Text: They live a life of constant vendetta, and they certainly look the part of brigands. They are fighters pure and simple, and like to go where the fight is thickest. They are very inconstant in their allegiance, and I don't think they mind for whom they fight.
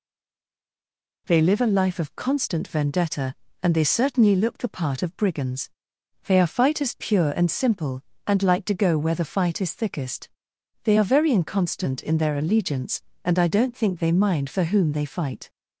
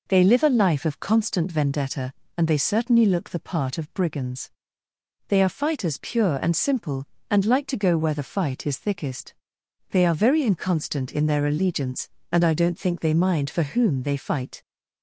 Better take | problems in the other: second | stays silent before the first word; noticeable; until 1.2 s; 1.2 s long

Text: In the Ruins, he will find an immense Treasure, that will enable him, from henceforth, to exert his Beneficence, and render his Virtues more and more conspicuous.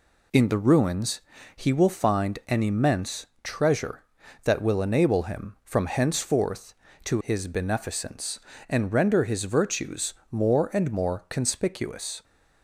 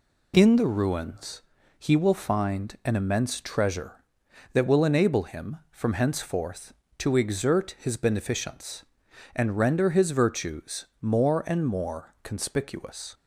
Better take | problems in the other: second | pauses between "immense" and "Treasure"; slight; at 3.2 s; 0.16 s long // skips "exert"; at 7.2 s // pauses between "Virtues" and "more"; slight; at 10.1 s; 0.16 s long

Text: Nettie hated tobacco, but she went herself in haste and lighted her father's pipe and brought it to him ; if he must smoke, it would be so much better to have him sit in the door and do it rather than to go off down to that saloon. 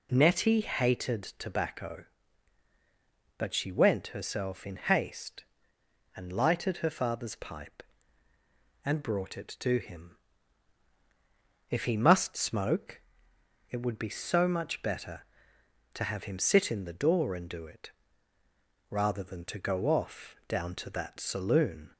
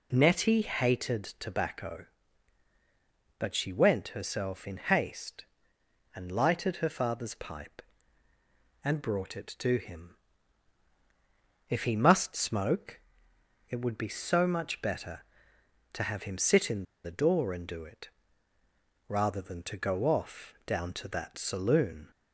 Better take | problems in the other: first | pauses between "hated" and "tobacco"; slight; at 1.2 s; 0.16 s long; slight in the first // pauses between "in" and "the"; slight; at 16.8 s; 0.21 s long // pauses between "it" and "rather"; at 18.0 s; 1.0 s long; also in the first

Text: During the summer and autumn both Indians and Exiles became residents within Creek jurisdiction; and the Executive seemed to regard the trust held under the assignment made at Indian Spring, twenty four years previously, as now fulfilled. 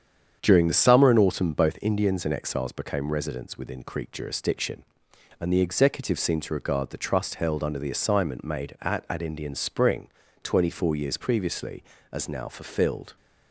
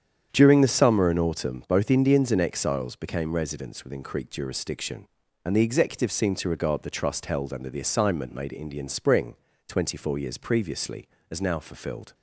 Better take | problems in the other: second | starts louder than the rest; strong; until 1.4 s; 8 dB; strong in the second // says "at" twice; at 9.0 s

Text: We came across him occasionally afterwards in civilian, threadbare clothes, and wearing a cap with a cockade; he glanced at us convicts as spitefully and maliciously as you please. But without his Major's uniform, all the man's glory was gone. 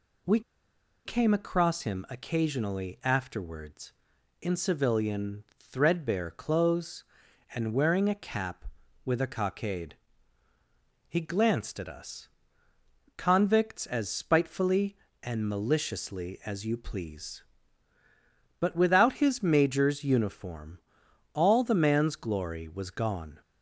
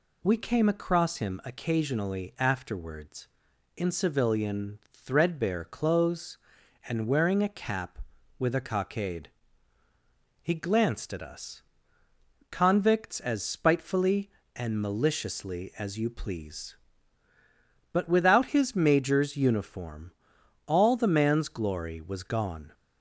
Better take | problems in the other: second | pauses between "We" and "came"; noticeable; at 0.4 s; 0.65 s long // pauses between "us" and "convicts"; noticeable; at 12.2 s; 0.88 s long; noticeable in the second

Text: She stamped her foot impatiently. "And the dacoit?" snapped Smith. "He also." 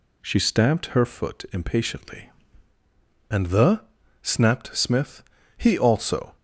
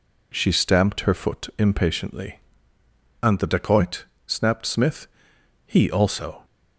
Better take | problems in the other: second | skips "dacoit"; at 4.0 s

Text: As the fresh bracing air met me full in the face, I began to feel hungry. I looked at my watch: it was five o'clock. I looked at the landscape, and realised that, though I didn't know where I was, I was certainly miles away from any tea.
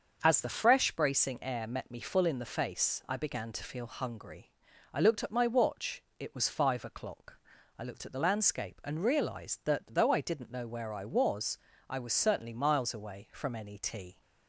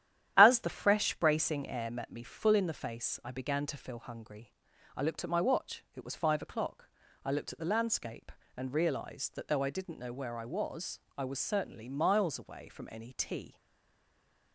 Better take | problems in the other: first | starts louder than the rest; strong; until 1.3 s; 11 dB; also in the first // stays silent after the last word; from 13.5 s on; 1.0 s long

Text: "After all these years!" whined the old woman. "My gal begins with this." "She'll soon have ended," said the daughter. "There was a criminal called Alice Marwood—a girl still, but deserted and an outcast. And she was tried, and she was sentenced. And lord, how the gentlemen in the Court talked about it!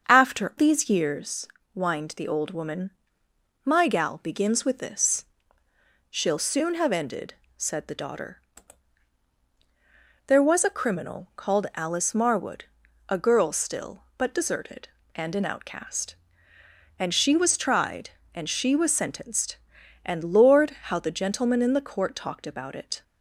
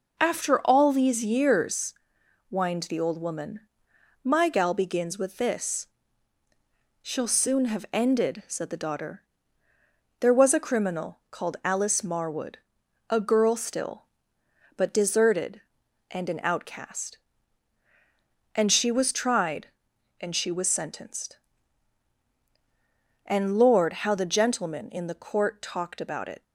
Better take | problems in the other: second | starts louder than the rest; until 1.1 s; 7 dB // skips "all"; at 0.5 s

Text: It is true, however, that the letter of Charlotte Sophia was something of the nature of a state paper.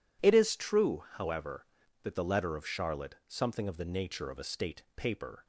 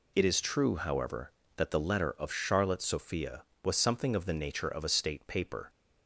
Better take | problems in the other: second | skips "Sophia was"; at 3.2 s

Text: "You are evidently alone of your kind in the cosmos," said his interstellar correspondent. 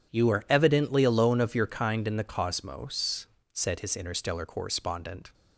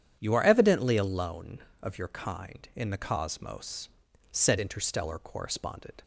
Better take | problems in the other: first | starts louder than the rest; strong; until 1.2 s; 9 dB // skips "his"; at 4.5 s

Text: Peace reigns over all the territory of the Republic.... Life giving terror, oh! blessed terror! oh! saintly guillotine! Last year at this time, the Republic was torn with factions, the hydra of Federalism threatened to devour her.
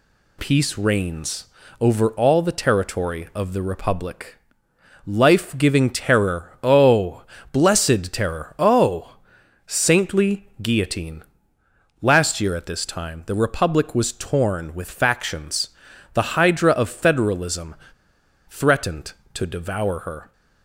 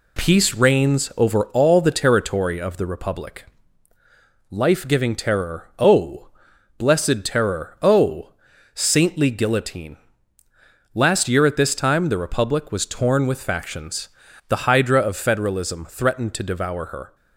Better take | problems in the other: second | pauses between "reigns" and "over"; slight; at 1.4 s; 0.34 s long // pauses between "Federalism" and "threatened"; noticeable; at 17.7 s; 0.74 s long

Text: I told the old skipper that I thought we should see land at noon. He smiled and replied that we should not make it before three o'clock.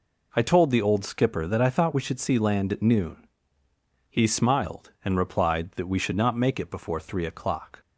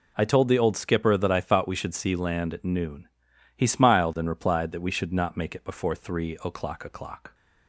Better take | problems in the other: first | says "o'clock" twice; at 6.8 s

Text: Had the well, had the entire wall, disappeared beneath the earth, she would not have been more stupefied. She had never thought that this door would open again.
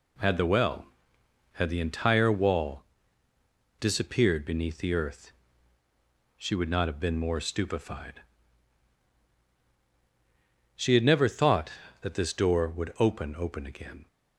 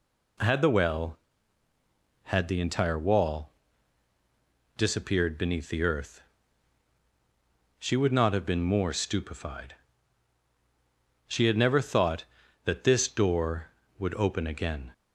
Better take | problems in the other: second | says "open" twice; at 13.3 s

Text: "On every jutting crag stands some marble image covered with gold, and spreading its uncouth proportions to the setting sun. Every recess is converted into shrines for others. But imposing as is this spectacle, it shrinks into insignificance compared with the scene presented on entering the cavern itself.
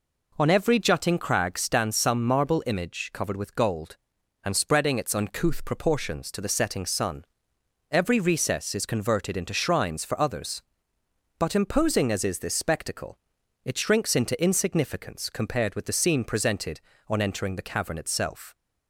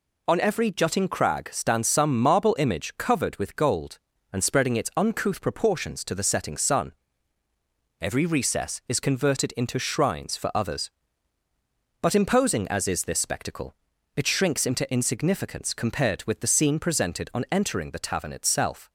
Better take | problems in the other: first | says "tavern" for "cavern"; at 18.0 s

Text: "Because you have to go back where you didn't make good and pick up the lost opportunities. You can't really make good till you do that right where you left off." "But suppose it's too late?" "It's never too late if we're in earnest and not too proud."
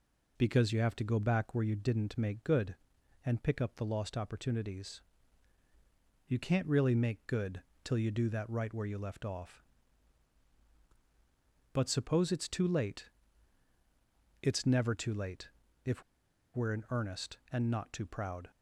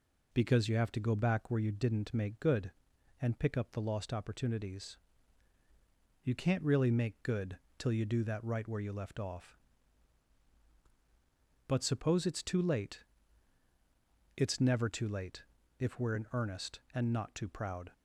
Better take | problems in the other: second | pauses between "good" and "till"; slight; at 7.6 s; 0.22 s long; slight in the second // pauses between "late" and "if"; at 15.4 s; 0.38 s long; also in the second // pauses between "if" and "we're"; noticeable; at 16.0 s; 0.51 s long

